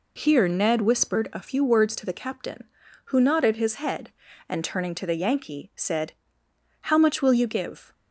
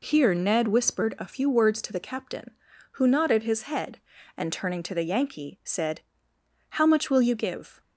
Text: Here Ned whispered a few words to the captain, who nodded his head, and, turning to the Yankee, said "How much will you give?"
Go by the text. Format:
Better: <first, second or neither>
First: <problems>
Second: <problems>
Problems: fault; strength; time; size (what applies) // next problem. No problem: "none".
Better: neither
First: pauses between "said" and "How"; noticeable; at 6.1 s; 0.70 s long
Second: pauses between "said" and "How"; noticeable; at 6.0 s; 0.70 s long